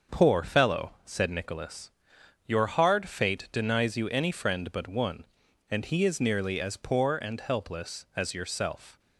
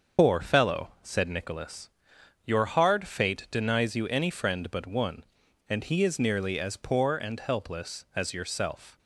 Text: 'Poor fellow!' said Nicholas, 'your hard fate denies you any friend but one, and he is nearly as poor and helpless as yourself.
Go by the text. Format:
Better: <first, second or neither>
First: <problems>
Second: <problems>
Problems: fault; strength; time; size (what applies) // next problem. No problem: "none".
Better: first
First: starts louder than the rest; until 1.2 s; 6.5 dB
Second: loses the start of "Poor"; at 0.1 s; 105 ms // starts louder than the rest; until 1.3 s; 6.5 dB